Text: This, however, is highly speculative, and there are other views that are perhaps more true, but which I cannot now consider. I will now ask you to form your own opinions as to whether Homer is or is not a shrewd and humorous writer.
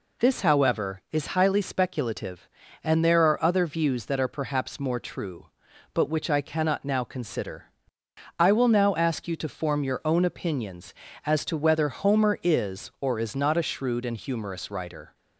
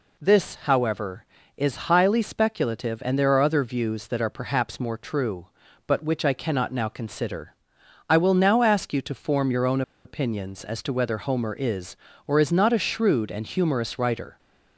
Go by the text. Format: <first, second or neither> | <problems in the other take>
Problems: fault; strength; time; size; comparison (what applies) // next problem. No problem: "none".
first | pauses between "own" and "opinions"; slight; at 9.8 s; 0.23 s long